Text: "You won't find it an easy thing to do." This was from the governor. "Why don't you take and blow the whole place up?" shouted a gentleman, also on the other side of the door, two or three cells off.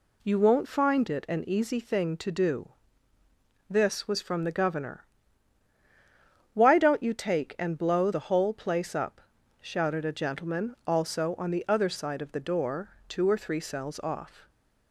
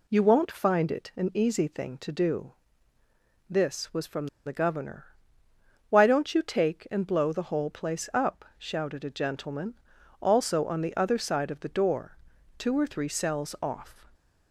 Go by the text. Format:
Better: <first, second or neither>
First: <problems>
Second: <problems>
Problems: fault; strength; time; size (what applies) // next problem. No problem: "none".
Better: first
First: none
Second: pauses between "from" and "the"; slight; at 4.2 s; 0.18 s long